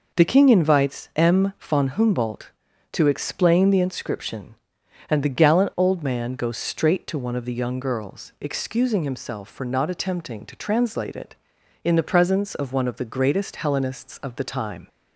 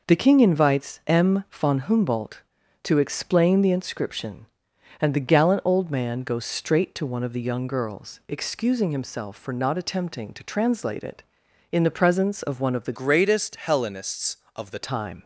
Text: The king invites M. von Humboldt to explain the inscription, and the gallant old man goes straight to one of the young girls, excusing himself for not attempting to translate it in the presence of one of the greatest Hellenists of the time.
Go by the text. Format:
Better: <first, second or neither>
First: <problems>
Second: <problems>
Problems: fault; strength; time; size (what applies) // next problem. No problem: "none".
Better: first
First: none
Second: changes voice from "greatest" to "the"; from 12.9 to 14.7 s; 1.8 s long